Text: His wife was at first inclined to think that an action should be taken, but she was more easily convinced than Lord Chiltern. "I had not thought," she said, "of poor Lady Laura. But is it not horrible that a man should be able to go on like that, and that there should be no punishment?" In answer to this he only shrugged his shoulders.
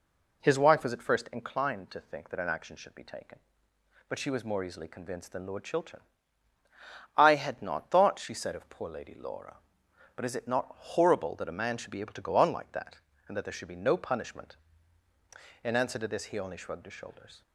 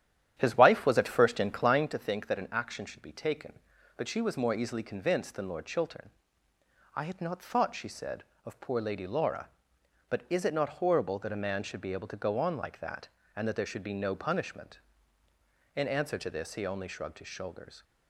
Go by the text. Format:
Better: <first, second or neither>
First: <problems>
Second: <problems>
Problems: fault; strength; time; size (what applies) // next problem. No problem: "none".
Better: first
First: none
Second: starts louder than the rest; strong; until 1.9 s; 10.5 dB